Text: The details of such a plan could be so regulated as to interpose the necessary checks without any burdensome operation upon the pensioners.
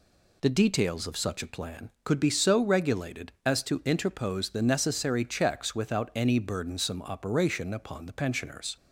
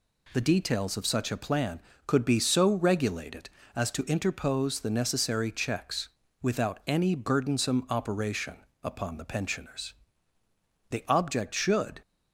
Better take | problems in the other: first | pauses between "checks" and "without"; slight; at 6.0 s; 0.32 s long // pauses between "operation" and "upon"; slight; at 8.5 s; 0.26 s long // goes on to say "The object should"; noticeable; from 10.8 s on; 1.1 s long

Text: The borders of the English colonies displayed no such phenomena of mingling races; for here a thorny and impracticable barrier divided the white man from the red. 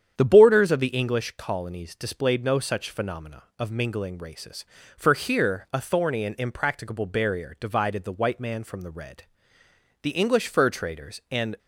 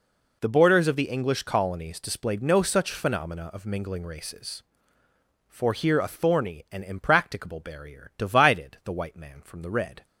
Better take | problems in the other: second | starts louder than the rest; strong; until 1.2 s; 8.5 dB // goes on to say "The English fur traders and"; from 10.0 s on; 1.5 s long

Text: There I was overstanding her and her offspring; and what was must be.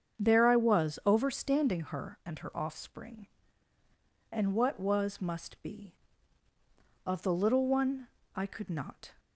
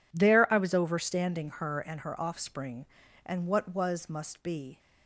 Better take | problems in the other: second | starts louder than the rest; strong; until 1.2 s; 7.5 dB // goes on to say "Of the little one I could not"; strong; from 7.0 s on; 2.1 s long

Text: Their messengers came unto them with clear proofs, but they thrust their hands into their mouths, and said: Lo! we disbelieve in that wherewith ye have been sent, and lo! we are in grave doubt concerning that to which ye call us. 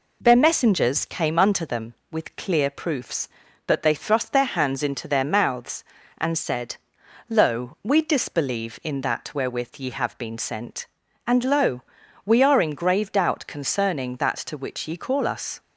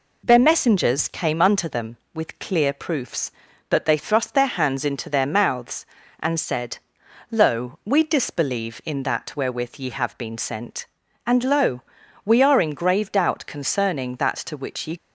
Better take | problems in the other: first | stops before "call us"; at 14.9 s

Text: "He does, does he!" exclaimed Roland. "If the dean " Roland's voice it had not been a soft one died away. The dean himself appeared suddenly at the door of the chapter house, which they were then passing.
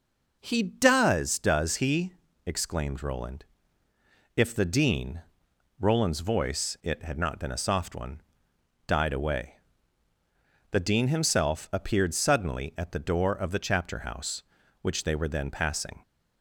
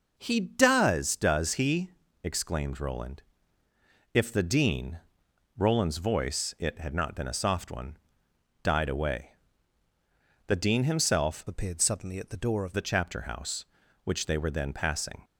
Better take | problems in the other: first | pauses between "one" and "died"; noticeable; at 7.9 s; 0.66 s long; noticeable in the first // changes voice from "appeared" to "of"; from 11.4 to 12.7 s; 1.3 s long

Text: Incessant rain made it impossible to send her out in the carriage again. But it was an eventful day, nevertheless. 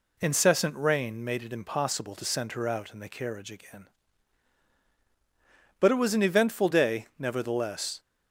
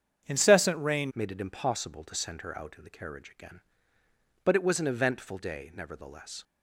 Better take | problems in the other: first | starts louder than the rest; strong; until 1.3 s; 7.5 dB // changes voice at "made"; from 1.1 s on; 5.3 s long

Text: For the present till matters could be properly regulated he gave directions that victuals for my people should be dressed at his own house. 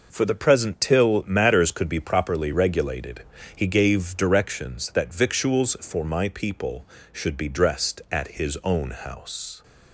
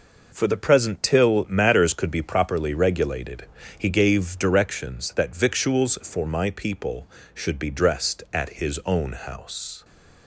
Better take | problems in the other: neither | pauses between "regulated" and "he"; slight; the same in both // pauses between "at" and "his"; slight; the same in both

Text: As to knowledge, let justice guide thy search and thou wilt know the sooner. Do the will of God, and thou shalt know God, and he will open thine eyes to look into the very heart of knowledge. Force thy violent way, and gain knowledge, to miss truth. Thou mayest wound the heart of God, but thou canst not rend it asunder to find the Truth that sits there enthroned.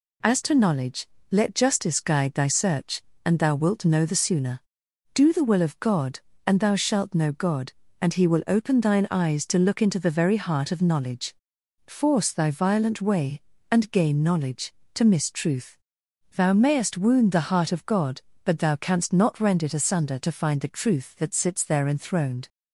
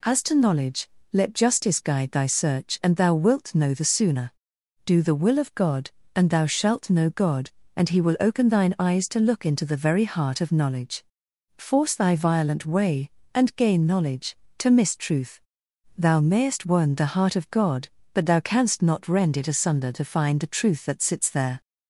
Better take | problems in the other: first | stops before "enthroned"; at 21.6 s

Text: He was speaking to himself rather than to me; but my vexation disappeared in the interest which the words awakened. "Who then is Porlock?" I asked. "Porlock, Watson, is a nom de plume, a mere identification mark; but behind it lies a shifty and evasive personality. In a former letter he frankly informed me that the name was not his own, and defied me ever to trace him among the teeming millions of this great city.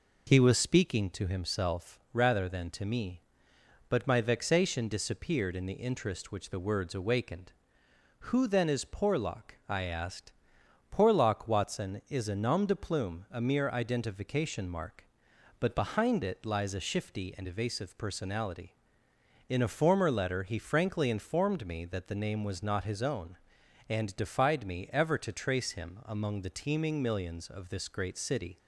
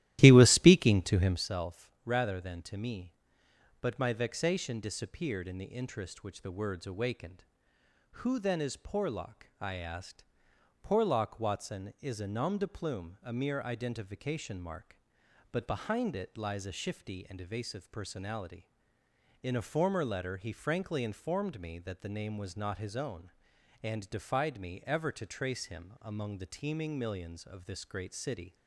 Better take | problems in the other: first | starts louder than the rest; strong; until 1.5 s; 14.5 dB

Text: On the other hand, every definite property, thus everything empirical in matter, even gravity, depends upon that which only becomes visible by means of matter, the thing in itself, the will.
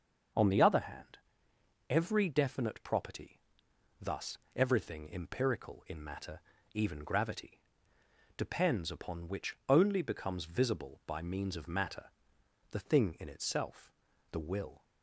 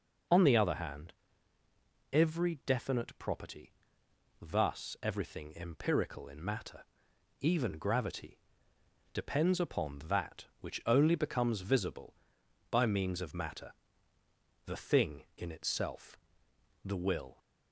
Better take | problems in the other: second | starts louder than the rest; until 2.0 s; 6.5 dB // pauses between "thus" and "everything"; slight; at 4.3 s; 0.18 s long // skips "that"; at 9.2 s

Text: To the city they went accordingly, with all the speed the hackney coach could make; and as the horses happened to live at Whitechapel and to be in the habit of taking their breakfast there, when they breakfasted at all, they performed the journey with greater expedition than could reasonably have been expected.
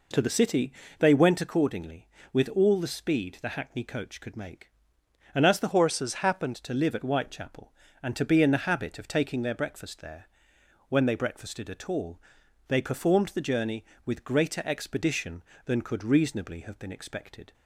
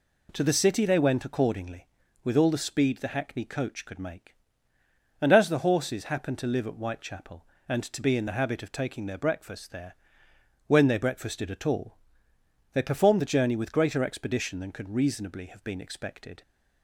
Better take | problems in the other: second | pauses between "city" and "they"; slight; at 0.7 s; 0.26 s long // changes voice from "horses" to "happened"; from 5.7 to 6.5 s; 0.8 s long

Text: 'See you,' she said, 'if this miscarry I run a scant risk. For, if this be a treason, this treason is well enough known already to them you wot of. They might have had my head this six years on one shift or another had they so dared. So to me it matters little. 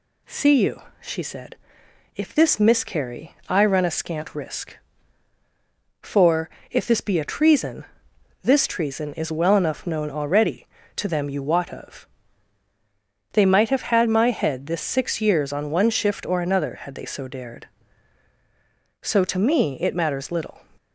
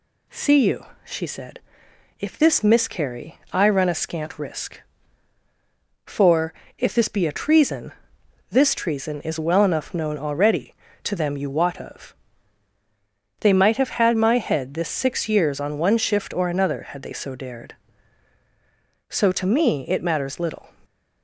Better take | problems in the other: neither | none

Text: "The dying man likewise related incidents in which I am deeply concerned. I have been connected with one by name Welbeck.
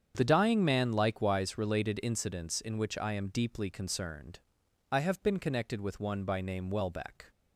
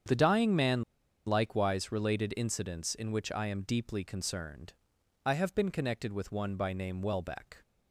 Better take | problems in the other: first | starts louder than the rest; strong; until 1.5 s; 8 dB; strong in the first // pauses between "man" and "likewise"; at 0.8 s; 0.44 s long

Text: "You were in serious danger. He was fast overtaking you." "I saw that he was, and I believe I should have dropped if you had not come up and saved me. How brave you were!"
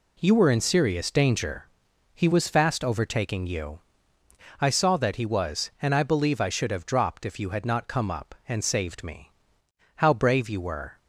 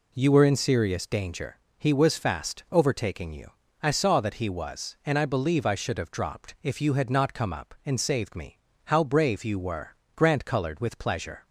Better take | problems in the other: first | goes on to say "Grant colored with pleasure"; noticeable; from 10.1 s on; 1.3 s long

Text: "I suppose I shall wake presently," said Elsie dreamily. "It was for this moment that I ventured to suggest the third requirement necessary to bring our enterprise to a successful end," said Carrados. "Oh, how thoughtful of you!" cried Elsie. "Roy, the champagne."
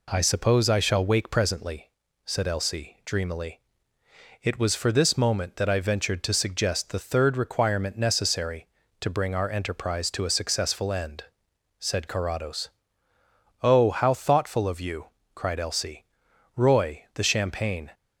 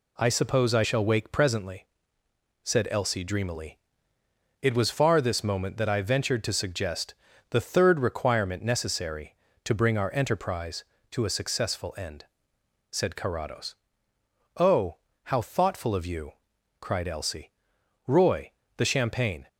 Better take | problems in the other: first | says "far" for "for"; at 4.9 s // pauses between "suggest" and "the"; slight; at 7.1 s; 0.34 s long

